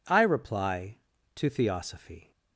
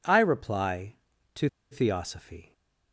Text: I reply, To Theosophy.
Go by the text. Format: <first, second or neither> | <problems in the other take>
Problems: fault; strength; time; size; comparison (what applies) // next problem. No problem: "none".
first | pauses between "To" and "Theosophy"; slight; at 1.4 s; 0.24 s long